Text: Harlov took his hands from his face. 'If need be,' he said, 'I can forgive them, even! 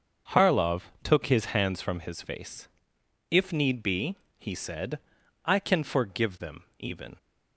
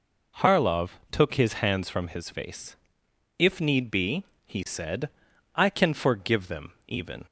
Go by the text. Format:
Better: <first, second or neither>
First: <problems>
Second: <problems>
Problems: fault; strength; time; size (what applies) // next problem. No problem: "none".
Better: second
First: gets quieter; strong; throughout; 11.5 dB // pauses between "Harlov" and "took"; slight; at 0.8 s; 0.22 s long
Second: pauses between "Harlov" and "took"; slight; at 0.8 s; 0.22 s long